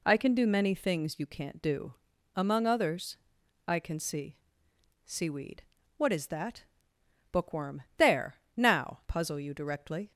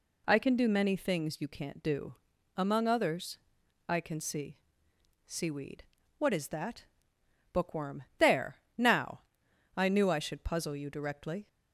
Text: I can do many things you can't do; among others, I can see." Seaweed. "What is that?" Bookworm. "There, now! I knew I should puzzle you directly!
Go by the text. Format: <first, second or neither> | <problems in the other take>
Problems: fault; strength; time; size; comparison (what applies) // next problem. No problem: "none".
second | skips "I knew I should"; at 9.0 s